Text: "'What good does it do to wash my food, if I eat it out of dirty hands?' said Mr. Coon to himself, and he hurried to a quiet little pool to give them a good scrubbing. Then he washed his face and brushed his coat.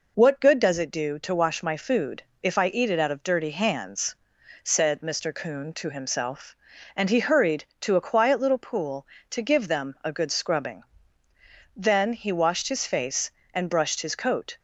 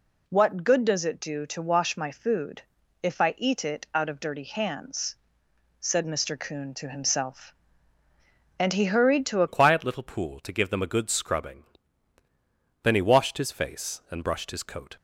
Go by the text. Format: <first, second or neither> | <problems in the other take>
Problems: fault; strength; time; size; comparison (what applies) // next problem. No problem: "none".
first | changes voice at "quiet"; from 9.4 s on; 5.5 s long